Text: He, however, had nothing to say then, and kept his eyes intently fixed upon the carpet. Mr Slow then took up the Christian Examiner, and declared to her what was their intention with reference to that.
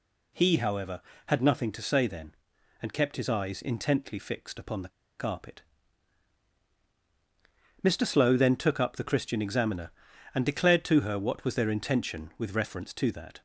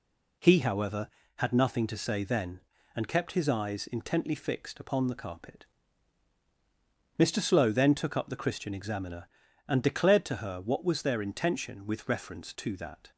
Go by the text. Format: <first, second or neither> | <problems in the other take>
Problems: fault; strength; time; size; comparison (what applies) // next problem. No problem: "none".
second | pauses between "the" and "carpet"; slight; at 4.8 s; 0.29 s long